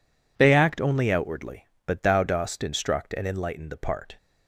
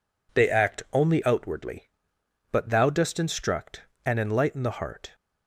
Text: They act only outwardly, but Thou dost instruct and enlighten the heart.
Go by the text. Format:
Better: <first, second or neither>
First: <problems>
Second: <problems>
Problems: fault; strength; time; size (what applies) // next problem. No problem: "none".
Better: second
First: says "part" for "heart"; at 3.7 s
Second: none